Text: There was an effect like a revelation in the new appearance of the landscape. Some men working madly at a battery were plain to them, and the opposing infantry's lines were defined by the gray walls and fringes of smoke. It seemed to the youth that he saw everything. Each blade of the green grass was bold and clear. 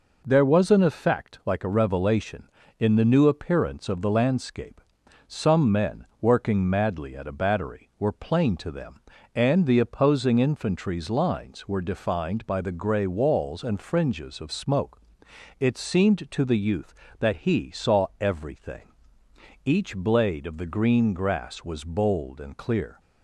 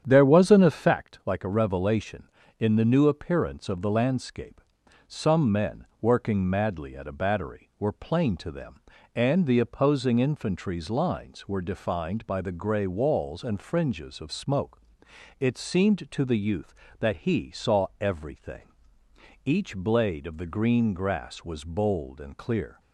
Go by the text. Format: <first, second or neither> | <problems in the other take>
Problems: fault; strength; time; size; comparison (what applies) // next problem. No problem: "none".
first | starts louder than the rest; strong; until 1.0 s; 9 dB